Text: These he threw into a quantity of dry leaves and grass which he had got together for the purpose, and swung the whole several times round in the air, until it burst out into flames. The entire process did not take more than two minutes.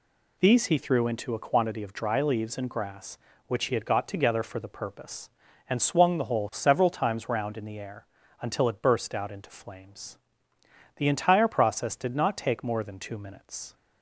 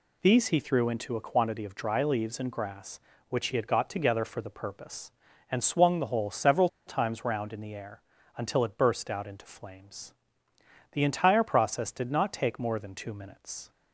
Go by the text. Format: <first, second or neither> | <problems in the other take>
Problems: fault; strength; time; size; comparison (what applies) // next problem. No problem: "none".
first | pauses between "several" and "times"; slight; at 6.6 s; 0.19 s long